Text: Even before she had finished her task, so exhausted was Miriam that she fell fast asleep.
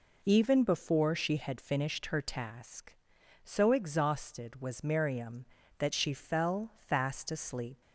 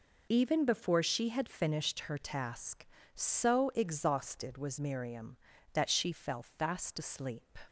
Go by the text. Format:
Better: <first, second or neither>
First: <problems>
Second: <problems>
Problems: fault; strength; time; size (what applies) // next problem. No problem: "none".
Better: neither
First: none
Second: none